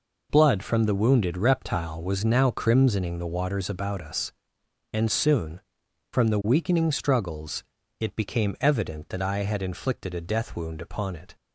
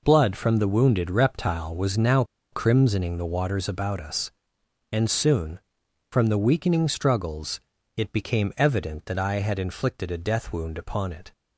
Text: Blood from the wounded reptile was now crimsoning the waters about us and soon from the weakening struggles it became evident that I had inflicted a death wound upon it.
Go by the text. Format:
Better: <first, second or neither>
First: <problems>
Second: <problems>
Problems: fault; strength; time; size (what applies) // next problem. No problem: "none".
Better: first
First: pauses between "struggles" and "it"; slight; at 7.6 s; 0.36 s long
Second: pauses between "now" and "crimsoning"; slight; at 2.2 s; 0.28 s long // pauses between "struggles" and "it"; slight; at 7.5 s; 0.36 s long